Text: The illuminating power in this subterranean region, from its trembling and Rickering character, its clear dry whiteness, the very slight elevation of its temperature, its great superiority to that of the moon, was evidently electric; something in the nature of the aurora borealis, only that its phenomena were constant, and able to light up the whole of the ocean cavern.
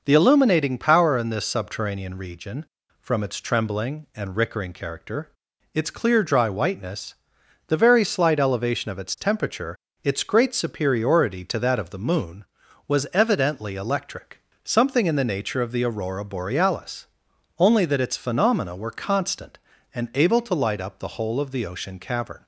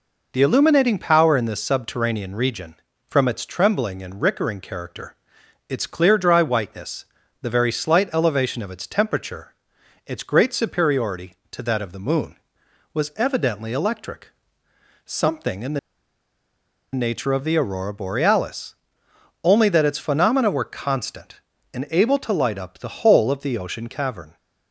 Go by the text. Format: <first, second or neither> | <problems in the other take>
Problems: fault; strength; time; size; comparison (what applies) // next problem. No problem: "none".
first | pauses between "the" and "nature"; at 15.7 s; 1.1 s long